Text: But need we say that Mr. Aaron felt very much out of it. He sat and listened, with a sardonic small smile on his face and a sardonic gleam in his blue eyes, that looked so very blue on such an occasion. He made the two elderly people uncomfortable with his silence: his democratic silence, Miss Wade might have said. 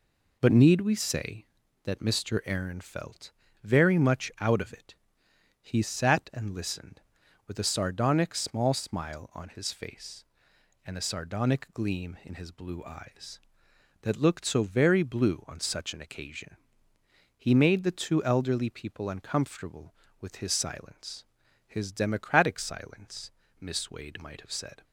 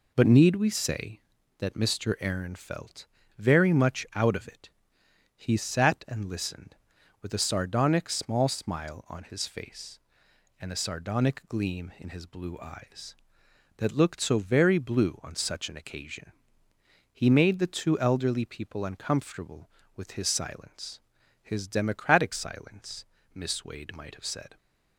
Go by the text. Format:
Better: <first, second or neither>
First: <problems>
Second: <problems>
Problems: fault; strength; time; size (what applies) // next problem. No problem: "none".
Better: neither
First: pauses between "felt" and "very"; slight; at 3.3 s; 0.32 s long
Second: pauses between "felt" and "very"; slight; at 3.0 s; 0.32 s long